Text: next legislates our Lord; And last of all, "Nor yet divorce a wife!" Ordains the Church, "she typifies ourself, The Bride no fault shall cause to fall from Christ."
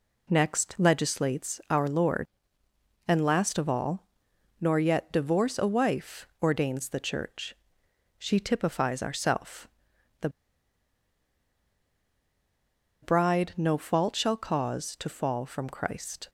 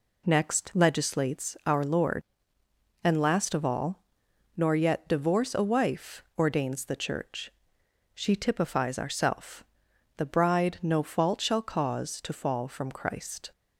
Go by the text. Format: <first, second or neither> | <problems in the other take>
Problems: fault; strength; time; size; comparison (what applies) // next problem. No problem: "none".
second | pauses between "The" and "Bride"; strong; at 10.2 s; 2.7 s long